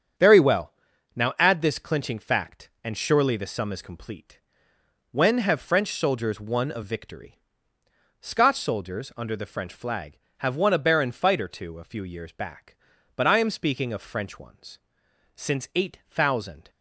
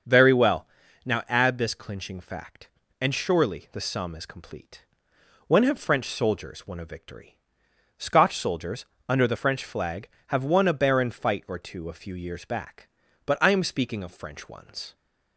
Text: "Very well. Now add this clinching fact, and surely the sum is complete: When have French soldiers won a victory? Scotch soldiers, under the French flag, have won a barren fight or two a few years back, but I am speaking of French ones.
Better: second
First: starts louder than the rest; strong; until 1.6 s; 7.5 dB // goes on to say "Since eight thousand"; from 15.3 s on; 1.3 s long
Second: starts louder than the rest; until 1.5 s; 7 dB

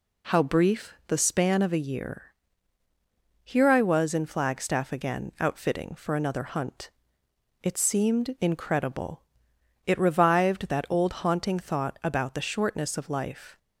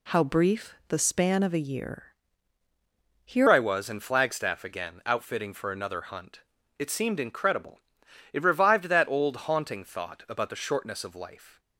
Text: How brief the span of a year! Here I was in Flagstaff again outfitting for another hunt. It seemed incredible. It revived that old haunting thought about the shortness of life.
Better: first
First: none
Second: changes voice at "I"; from 3.4 s on; 8.1 s long

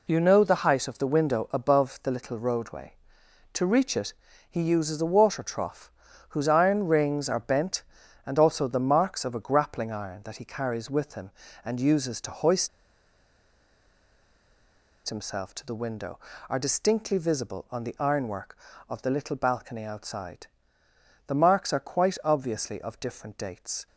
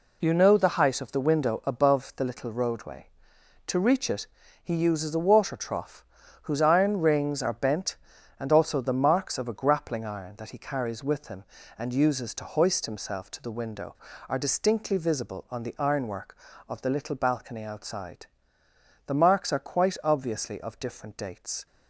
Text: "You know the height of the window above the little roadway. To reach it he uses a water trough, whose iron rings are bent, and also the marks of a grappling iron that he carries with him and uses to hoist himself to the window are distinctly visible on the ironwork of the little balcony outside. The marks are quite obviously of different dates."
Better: second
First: pauses between "it" and "he"; slight; at 4.1 s; 0.36 s long // pauses between "hoist" and "himself"; strong; at 12.6 s; 2.3 s long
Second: pauses between "it" and "he"; slight; at 4.2 s; 0.36 s long

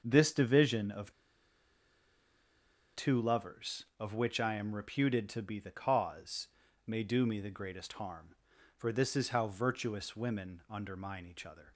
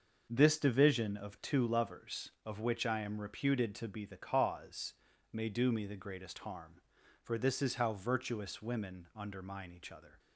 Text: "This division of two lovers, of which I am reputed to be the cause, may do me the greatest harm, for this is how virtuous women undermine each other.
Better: second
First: starts louder than the rest; until 1.0 s; 6 dB // pauses between "of" and "two"; strong; at 1.1 s; 1.8 s long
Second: starts louder than the rest; until 1.3 s; 6 dB

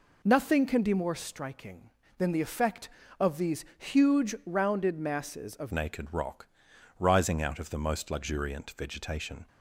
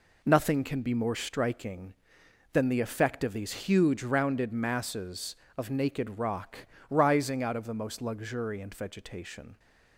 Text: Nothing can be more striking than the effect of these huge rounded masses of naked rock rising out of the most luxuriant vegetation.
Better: second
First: changes voice at "naked"; from 5.7 s on; 3.7 s long // pauses between "rock" and "rising"; noticeable; at 6.4 s; 0.52 s long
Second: pauses between "rock" and "rising"; slight; at 6.5 s; 0.32 s long

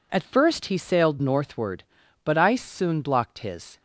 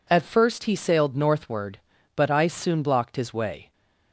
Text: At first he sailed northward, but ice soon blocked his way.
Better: second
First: stops before "way"; at 3.7 s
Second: none

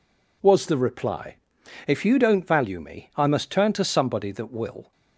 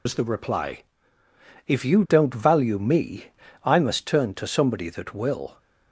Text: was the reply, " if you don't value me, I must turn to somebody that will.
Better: first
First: none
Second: loses the start of "was"; at 0.0 s; 70 ms

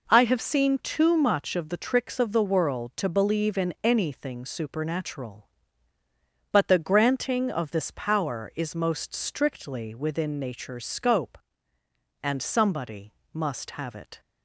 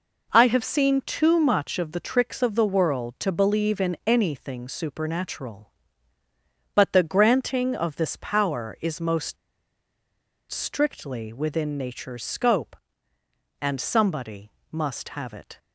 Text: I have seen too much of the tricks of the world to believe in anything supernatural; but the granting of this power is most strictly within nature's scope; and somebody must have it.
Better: first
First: pauses between "somebody" and "must"; slight; at 13.1 s; 0.18 s long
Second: pauses between "most" and "strictly"; at 9.3 s; 1.1 s long // pauses between "somebody" and "must"; slight; at 14.5 s; 0.18 s long

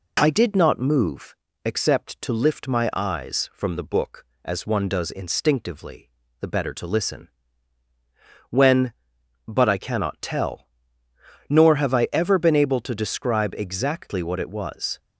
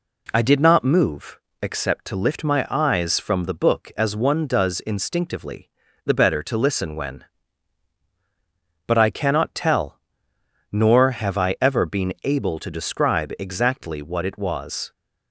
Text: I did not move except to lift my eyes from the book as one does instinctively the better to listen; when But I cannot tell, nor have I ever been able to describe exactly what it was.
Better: neither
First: pauses between "move" and "except"; slight; at 1.3 s; 0.28 s long // pauses between "instinctively" and "the"; slight; at 6.1 s; 0.30 s long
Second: pauses between "move" and "except"; slight; at 1.3 s; 0.22 s long // pauses between "instinctively" and "the"; slight; at 5.6 s; 0.36 s long

